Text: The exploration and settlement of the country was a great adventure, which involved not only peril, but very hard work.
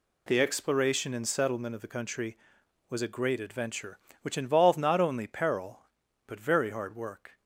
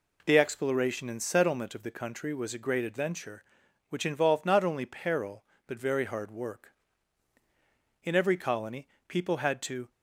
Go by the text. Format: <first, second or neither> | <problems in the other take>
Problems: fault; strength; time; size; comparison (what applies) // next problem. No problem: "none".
first | goes on to say "In every colony people had to"; strong; from 8.0 s on; 1.8 s long